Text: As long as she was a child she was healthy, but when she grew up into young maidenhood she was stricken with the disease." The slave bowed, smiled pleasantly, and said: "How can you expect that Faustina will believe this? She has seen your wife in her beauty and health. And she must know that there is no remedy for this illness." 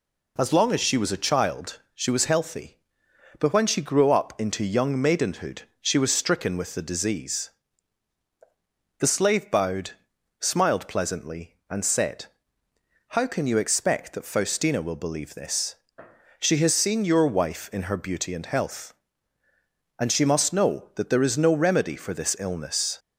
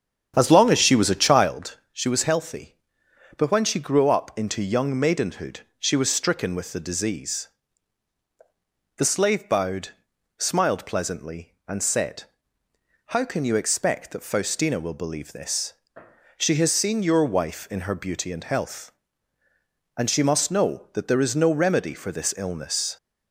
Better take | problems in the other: first | starts louder than the rest; strong; until 1.6 s; 8.5 dB // pauses between "child" and "she"; slight; at 1.7 s; 0.16 s long; slight in the first // pauses between "maidenhood" and "she"; slight; at 5.6 s; 0.18 s long; slight in the first

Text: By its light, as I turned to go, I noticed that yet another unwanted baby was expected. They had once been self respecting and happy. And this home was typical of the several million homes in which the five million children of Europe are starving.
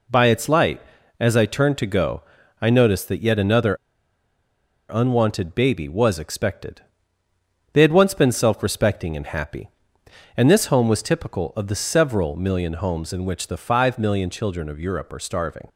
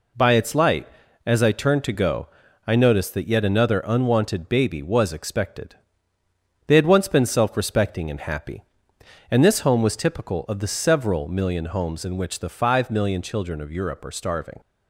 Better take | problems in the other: second | pauses between "another" and "unwanted"; at 3.7 s; 1.1 s long

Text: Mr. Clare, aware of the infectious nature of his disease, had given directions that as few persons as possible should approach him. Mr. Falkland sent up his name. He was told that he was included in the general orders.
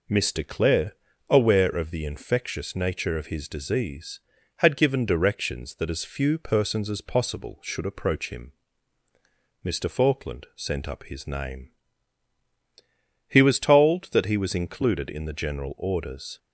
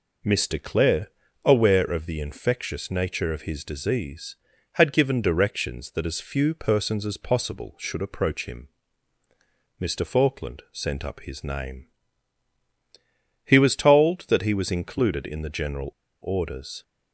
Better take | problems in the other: first | pauses between "general" and "orders"; slight; at 15.9 s; 0.30 s long

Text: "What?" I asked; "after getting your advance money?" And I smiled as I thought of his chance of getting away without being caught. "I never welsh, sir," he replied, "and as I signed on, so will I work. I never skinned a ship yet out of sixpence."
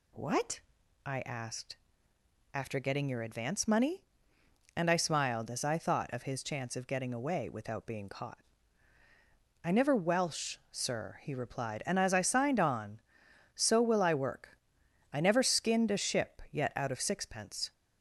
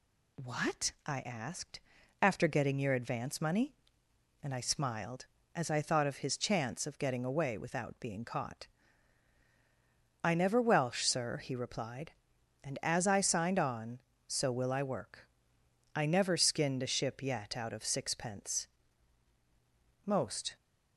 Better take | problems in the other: first | goes on to say "Most"; from 20.0 s on; 0.52 s long

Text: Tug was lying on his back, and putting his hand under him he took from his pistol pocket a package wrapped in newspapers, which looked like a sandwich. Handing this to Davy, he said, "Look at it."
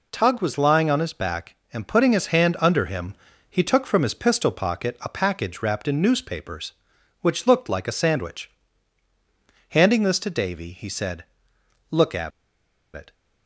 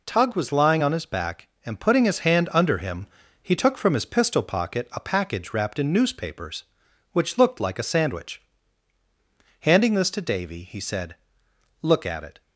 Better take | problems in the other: second | pauses between "him" and "he"; at 3.1 s; 0.38 s long; also in the second // pauses between "at" and "it"; noticeable; at 12.3 s; 0.64 s long

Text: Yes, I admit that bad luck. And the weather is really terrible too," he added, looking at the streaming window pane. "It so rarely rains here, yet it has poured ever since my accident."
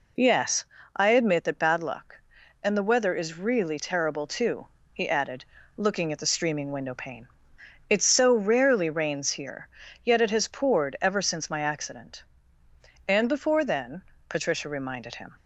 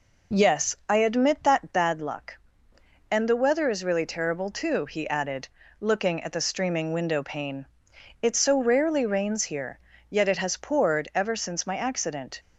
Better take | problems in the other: second | goes on to say "And before then Patricia reminded him"; strong; from 13.0 s on; 2.2 s long

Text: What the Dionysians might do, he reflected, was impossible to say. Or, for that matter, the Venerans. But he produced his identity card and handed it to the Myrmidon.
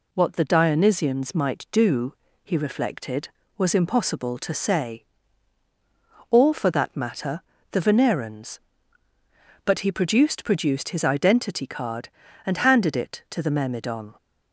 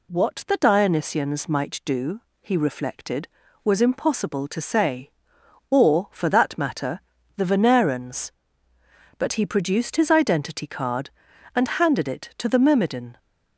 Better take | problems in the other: second | says "produced" twice; at 10.4 s

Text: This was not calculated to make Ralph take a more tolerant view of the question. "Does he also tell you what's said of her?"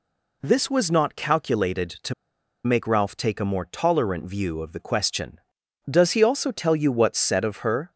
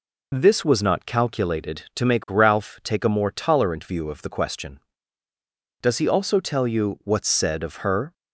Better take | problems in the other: second | pauses between "to" and "make"; noticeable; at 2.1 s; 0.51 s long

